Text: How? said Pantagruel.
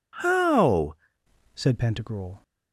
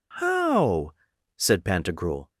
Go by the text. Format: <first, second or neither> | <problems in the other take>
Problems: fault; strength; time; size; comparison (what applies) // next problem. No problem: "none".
second | changes voice at "said"; from 1.5 s on; 0.9 s long